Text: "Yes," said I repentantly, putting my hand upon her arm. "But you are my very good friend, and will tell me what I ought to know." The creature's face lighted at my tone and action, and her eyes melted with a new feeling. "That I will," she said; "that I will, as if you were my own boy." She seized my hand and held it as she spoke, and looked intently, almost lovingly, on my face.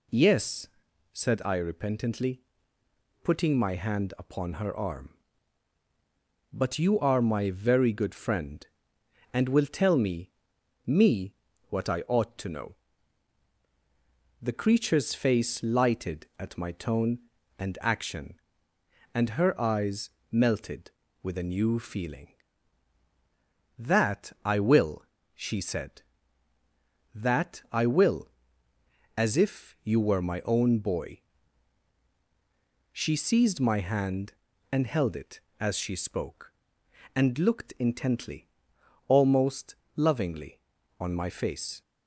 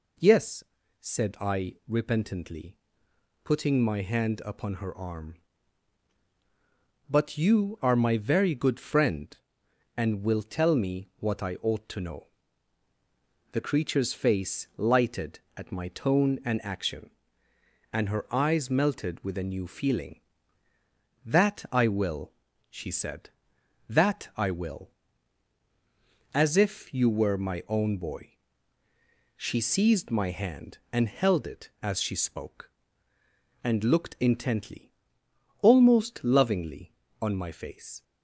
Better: second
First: says "me" twice; at 10.8 s // pauses between "eyes" and "melted"; slight; at 20.0 s; 0.22 s long // pauses between "almost" and "lovingly"; slight; at 39.7 s; 0.22 s long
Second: none

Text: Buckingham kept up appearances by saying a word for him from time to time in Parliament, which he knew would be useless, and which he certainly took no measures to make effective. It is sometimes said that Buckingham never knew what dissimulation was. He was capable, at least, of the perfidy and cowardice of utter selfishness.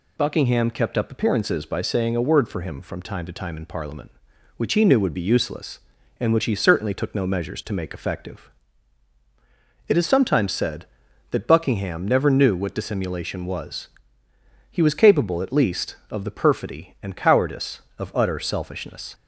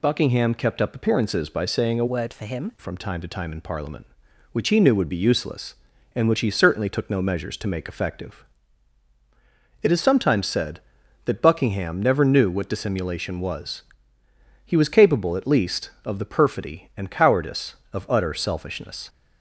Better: first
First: none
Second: changes voice from "word" to "him"; from 2.0 to 2.7 s; 0.7 s long

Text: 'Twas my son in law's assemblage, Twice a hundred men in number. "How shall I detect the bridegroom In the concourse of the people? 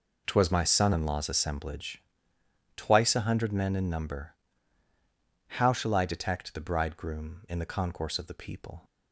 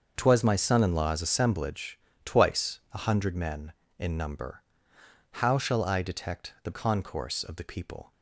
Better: first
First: none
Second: starts louder than the rest; until 1.1 s; 6.5 dB // skips "bridegroom In the"; at 6.7 s

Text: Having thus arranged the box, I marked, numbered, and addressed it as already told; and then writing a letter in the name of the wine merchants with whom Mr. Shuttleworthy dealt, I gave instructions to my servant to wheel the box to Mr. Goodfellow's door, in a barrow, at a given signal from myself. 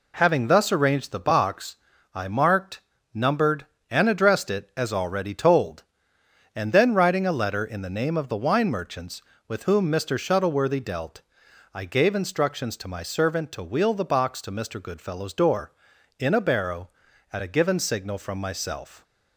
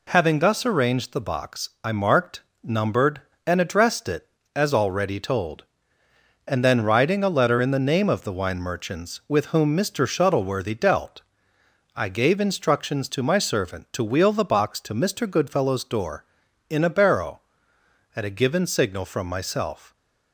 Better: neither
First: none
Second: none

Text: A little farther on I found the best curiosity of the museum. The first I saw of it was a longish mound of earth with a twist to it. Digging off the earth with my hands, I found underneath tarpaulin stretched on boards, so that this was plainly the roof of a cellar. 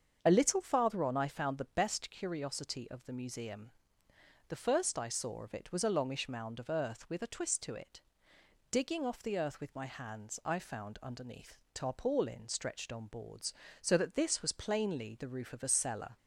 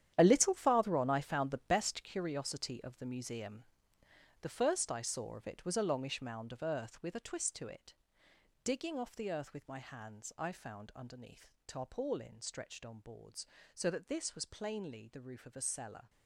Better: first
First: starts louder than the rest; strong; until 1.2 s; 7.5 dB // pauses between "underneath" and "tarpaulin"; slight; at 11.5 s; 0.16 s long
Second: gets quieter; strong; throughout; 12.5 dB // starts louder than the rest; strong; until 1.1 s; 10.5 dB // pauses between "underneath" and "tarpaulin"; slight; at 11.4 s; 0.16 s long

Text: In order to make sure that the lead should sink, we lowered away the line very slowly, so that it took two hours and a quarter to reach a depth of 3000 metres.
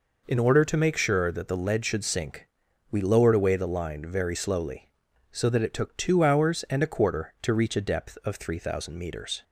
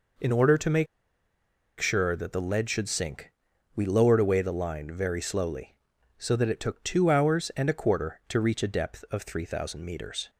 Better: first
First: none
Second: pauses between "make" and "sure"; noticeable; at 0.8 s; 0.93 s long

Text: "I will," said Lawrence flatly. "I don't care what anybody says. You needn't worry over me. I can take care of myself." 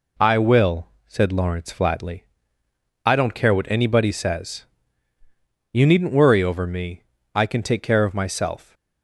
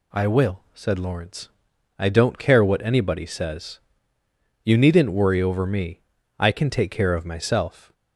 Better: first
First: none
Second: skips "flatly"; at 1.7 s

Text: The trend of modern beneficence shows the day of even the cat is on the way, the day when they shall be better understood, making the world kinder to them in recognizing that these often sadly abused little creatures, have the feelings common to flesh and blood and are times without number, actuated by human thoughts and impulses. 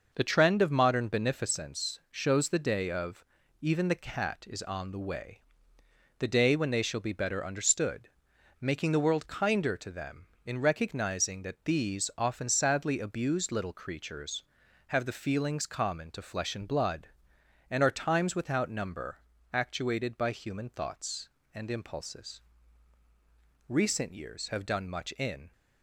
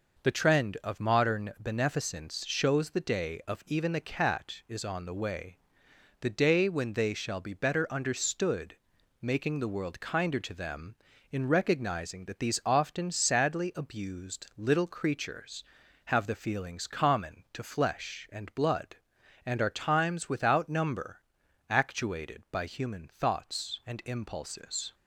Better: second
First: pauses between "of" and "even"; at 3.2 s; 0.38 s long // goes on to say "Recent years have done much in"; strong; from 23.6 s on; 1.8 s long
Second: none

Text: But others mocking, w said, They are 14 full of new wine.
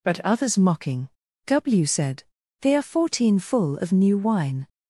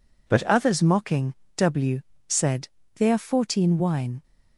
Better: first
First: none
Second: pauses between "w" and "said"; slight; at 2.0 s; 0.26 s long // skips "full of new"; at 3.7 s

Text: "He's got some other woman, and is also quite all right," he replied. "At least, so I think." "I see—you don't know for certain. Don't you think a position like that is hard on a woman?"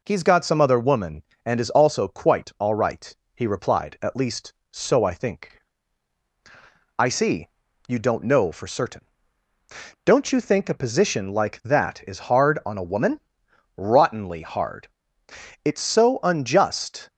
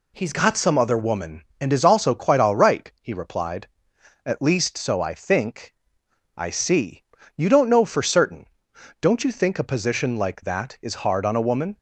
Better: second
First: goes on to say "Rottenly hard It's so unjust"; strong; from 13.7 s on; 3.3 s long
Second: none

